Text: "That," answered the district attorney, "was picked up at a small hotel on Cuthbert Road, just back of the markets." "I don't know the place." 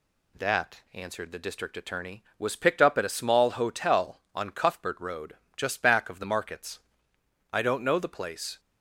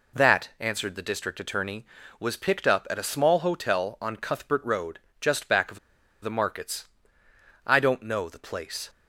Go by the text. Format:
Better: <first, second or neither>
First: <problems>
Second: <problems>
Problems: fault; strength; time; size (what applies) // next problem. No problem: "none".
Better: first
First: none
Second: pauses between "of" and "the"; at 5.7 s; 0.44 s long